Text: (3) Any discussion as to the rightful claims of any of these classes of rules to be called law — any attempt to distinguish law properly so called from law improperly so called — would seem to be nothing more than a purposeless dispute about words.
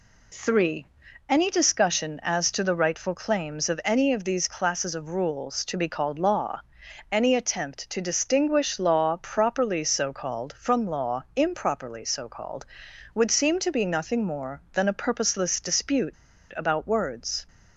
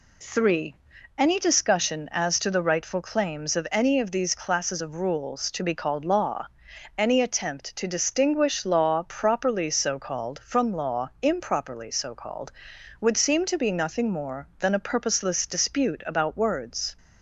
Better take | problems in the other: second | pauses between "dispute" and "about"; at 16.1 s; 0.41 s long

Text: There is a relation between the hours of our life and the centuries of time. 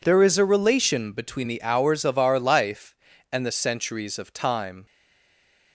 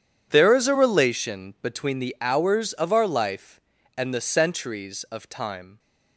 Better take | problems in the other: second | stays silent after the last word; slight; from 4.8 s on; 0.9 s long

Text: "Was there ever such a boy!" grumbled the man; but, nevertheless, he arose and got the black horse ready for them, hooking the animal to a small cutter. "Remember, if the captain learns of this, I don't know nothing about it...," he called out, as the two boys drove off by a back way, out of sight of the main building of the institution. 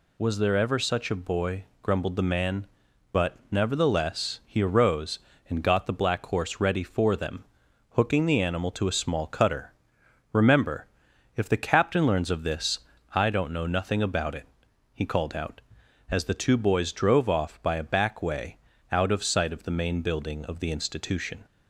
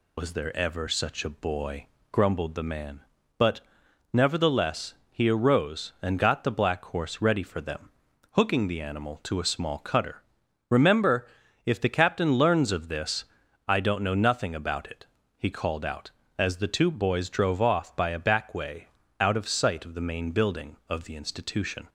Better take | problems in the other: first | loses the start of "Was"; at 0.1 s; 70 ms

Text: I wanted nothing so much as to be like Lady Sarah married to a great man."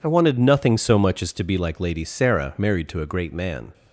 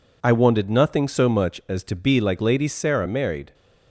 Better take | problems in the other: first | stops before "to a great man"; at 3.5 s

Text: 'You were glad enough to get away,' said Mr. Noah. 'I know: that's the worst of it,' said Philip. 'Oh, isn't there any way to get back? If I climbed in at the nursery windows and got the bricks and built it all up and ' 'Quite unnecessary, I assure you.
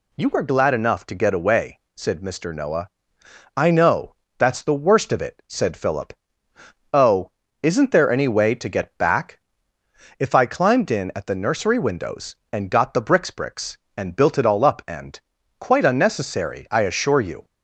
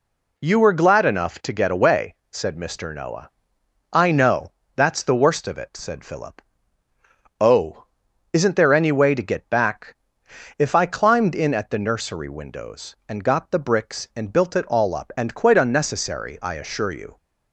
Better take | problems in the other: second | says "bricks" twice; at 13.2 s

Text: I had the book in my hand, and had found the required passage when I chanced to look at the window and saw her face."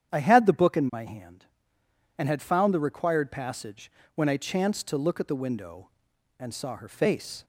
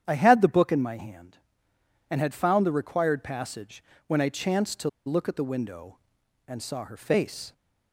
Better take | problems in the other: first | starts louder than the rest; strong; until 1.0 s; 9 dB; strong in the first // pauses between "passage" and "when"; slight; at 3.8 s; 0.24 s long; slight in the first // pauses between "to" and "look"; slight; at 4.8 s; 0.17 s long

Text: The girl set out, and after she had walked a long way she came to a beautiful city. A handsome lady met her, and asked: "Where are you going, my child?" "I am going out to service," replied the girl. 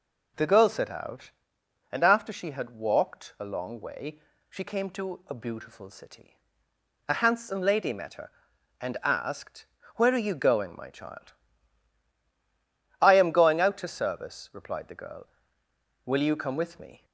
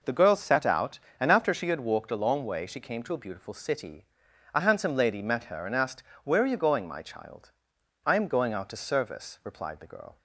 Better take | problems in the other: second | pauses between "way" and "she"; slight; at 4.1 s; 0.30 s long // goes on to say "Will you come with me"; noticeable; from 16.0 s on; 0.98 s long

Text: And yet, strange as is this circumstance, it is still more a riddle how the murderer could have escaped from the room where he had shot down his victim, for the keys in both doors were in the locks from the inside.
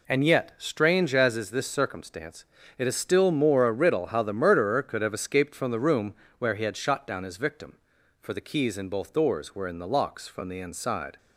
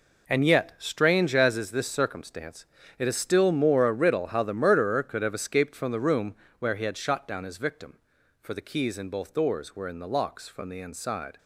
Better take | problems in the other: first | gets quieter; strong; throughout; 11 dB // pauses between "room" and "where"; slight; at 6.3 s; 0.26 s long; slight in the first

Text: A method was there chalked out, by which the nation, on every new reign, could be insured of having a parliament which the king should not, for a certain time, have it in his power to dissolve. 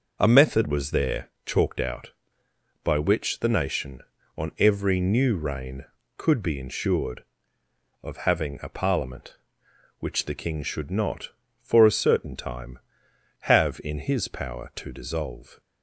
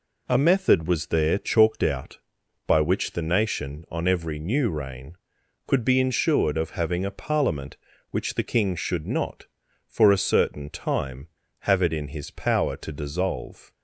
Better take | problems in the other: second | pauses between "there" and "chalked"; slight; at 1.3 s; 0.16 s long // skips "it"; at 13.8 s

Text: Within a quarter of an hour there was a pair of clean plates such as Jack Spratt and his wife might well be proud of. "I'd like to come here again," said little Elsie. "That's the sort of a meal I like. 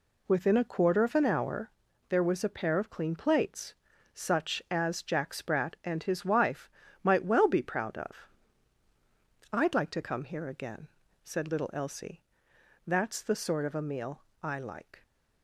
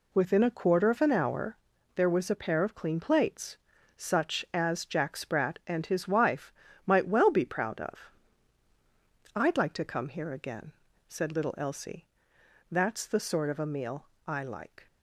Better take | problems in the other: neither | pauses between "hour" and "there"; the same in both // pauses between "plates" and "such"; slight; the same in both // pauses between "wife" and "might"; slight; the same in both // pauses between "meal" and "I"; slight; the same in both

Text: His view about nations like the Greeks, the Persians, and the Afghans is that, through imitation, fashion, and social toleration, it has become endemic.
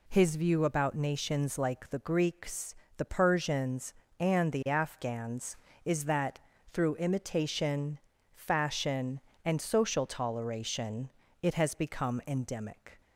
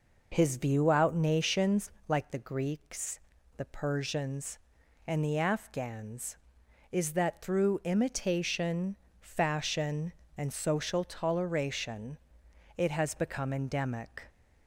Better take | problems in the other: first | says "out" for "about"; at 0.9 s // pauses between "nations" and "like"; slight; at 1.9 s; 0.18 s long

